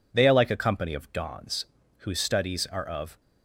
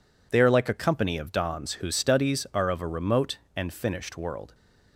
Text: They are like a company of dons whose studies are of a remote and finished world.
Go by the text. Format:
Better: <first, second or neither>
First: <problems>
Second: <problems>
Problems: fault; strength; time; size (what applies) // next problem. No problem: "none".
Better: second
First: pauses between "dons" and "whose"; at 1.6 s; 0.38 s long // stops before "a remote and finished world"; at 3.2 s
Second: none